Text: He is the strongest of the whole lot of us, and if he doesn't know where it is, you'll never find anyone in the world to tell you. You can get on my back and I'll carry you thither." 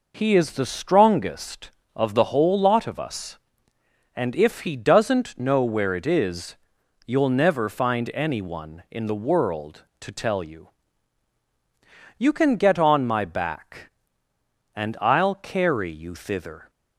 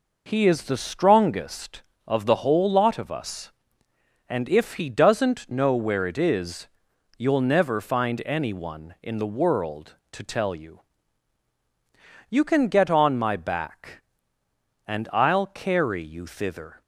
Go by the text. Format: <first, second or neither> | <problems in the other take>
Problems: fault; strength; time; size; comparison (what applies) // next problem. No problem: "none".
neither | none